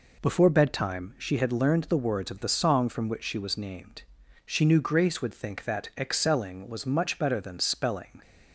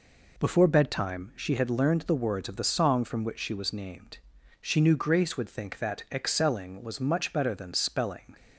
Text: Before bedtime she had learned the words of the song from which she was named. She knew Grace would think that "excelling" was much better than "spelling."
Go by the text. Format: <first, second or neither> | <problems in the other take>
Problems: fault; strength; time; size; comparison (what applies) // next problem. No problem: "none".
neither | none